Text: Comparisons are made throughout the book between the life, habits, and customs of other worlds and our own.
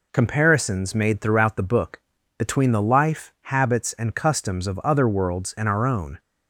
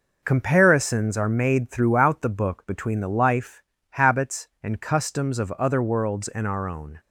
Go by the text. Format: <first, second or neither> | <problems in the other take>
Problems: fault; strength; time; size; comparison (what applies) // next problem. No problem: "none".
second | skips "are"; at 0.9 s // pauses between "book" and "between"; at 1.9 s; 0.40 s long